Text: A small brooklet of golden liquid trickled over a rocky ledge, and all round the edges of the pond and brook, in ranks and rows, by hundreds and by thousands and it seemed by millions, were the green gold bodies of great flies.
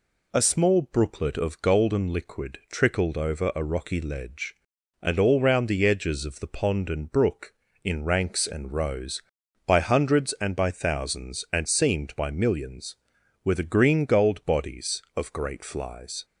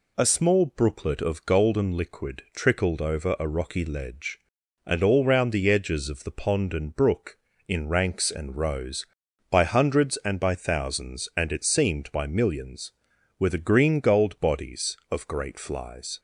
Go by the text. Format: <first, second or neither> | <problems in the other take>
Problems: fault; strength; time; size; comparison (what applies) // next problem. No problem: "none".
second | skips "it"; at 11.6 s